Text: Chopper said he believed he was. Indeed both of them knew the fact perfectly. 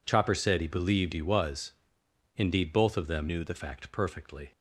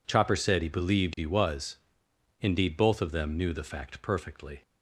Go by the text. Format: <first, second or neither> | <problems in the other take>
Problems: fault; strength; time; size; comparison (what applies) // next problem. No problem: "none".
second | changes voice from "knew" to "the"; from 3.2 to 3.5 s; 0.3 s long